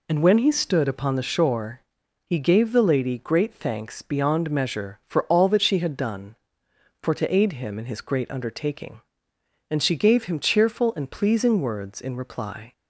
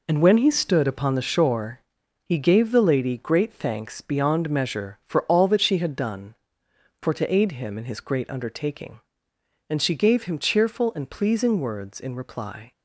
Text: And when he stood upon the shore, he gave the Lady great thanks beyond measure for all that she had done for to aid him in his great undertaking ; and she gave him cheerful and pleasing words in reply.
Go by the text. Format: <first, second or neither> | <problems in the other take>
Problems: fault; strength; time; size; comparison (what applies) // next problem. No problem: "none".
first | gets quieter; strong; throughout; 8 dB